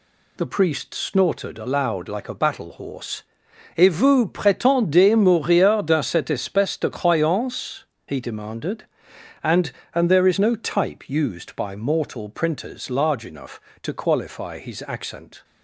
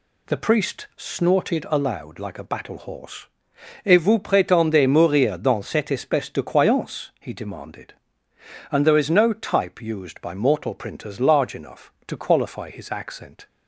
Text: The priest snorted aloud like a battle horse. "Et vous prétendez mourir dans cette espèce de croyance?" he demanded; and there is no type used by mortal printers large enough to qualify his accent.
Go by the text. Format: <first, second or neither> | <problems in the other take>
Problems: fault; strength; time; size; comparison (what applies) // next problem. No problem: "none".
second | says "and" twice; at 9.9 s